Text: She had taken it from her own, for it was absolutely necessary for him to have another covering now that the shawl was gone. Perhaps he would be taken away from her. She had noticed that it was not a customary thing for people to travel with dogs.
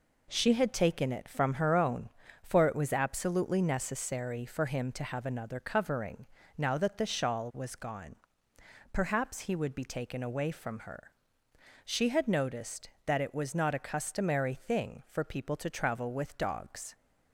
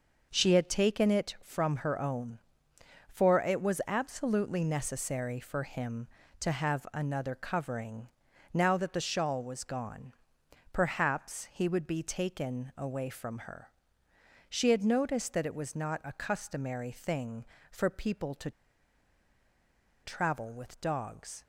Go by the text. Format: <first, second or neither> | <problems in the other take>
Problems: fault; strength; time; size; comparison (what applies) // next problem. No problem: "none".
first | pauses between "covering" and "now"; at 8.0 s; 0.44 s long; slight in the first // pauses between "to" and "travel"; strong; at 18.5 s; 1.5 s long